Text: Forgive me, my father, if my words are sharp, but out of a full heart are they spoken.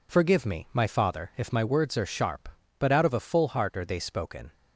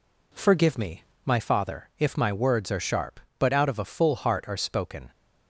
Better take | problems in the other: first | skips "they"; at 4.5 s

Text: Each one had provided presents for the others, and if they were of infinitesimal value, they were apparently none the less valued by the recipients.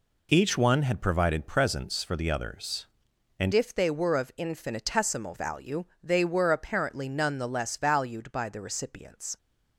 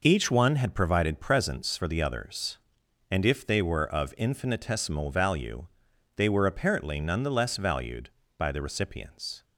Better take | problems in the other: second | changes voice at "if"; from 3.5 s on; 5.8 s long

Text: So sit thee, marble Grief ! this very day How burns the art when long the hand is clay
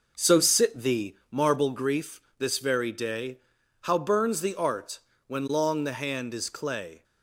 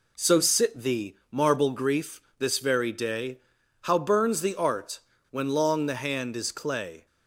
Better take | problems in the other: second | starts louder than the rest; noticeable; until 1.5 s; 5.5 dB // pauses between "day" and "How"; at 3.3 s; 0.44 s long; also in the second // pauses between "art" and "when"; slight; at 4.9 s; 0.26 s long; slight in the second

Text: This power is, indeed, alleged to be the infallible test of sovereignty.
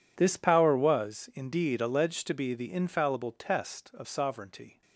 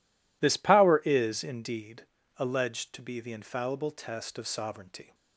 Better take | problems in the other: second | says "was" for "is"; at 0.7 s

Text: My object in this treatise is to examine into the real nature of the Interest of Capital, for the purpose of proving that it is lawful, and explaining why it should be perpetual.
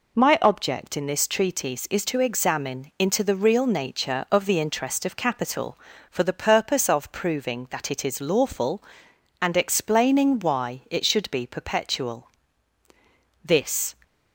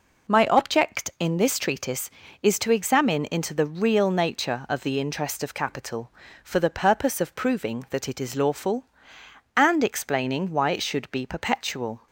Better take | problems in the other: second | goes on to say "This"; from 13.4 s on; 0.52 s long

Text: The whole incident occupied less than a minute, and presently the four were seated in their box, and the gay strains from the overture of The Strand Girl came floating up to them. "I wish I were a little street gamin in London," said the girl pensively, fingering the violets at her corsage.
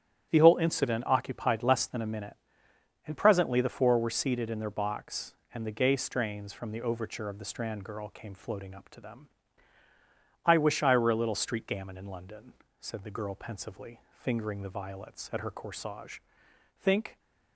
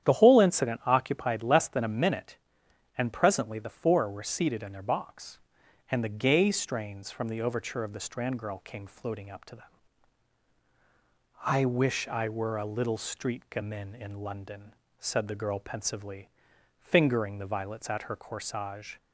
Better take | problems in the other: second | starts louder than the rest; strong; until 1.3 s; 10 dB; strong in the second // goes on to say "Think"; slight; from 16.7 s on; 0.40 s long

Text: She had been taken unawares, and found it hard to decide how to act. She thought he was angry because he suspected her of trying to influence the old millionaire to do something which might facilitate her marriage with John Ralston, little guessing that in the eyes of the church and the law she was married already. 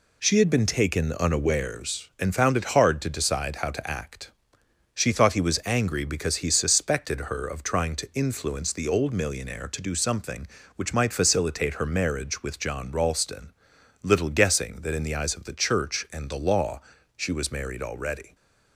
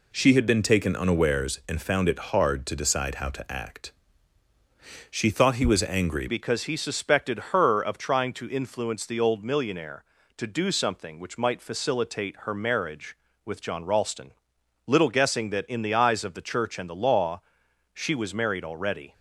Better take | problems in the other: first | changes voice at "because"; from 6.2 s on; 12.9 s long // pauses between "law" and "she"; noticeable; at 17.4 s; 0.52 s long; slight in the first

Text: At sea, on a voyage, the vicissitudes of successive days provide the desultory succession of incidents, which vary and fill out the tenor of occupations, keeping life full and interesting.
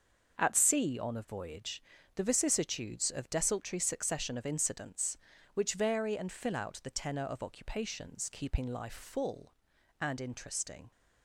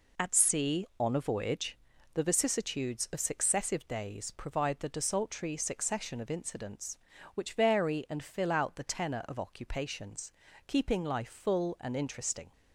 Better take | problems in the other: second | starts louder than the rest; until 1.4 s; 6.5 dB // skips "successive days provide the"; at 3.2 s

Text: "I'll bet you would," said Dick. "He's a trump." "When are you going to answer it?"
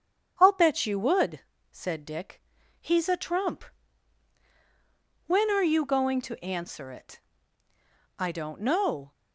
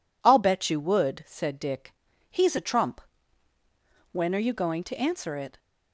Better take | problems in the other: second | starts louder than the rest; strong; until 1.3 s; 8 dB // goes on to say "I don't know"; noticeable; from 8.1 s on; 0.96 s long

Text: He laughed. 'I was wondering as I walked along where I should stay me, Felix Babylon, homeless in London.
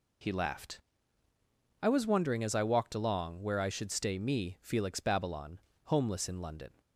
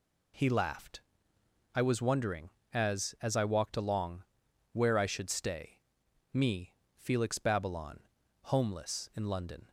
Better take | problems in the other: first | says "as" twice; at 3.2 s // pauses between "along" and "where"; noticeable; at 4.2 s; 0.48 s long // pauses between "stay" and "me"; noticeable; at 5.7 s; 0.54 s long

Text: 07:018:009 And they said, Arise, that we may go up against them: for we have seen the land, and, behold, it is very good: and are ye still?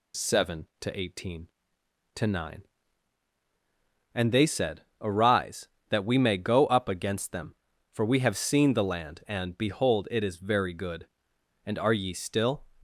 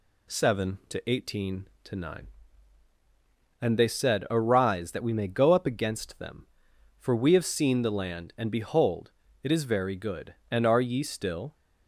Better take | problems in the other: neither | none

